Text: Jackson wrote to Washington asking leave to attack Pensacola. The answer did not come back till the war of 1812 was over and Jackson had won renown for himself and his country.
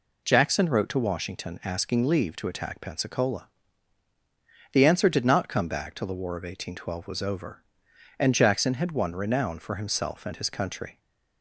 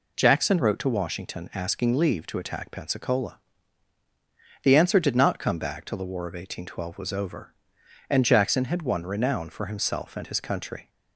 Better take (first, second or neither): neither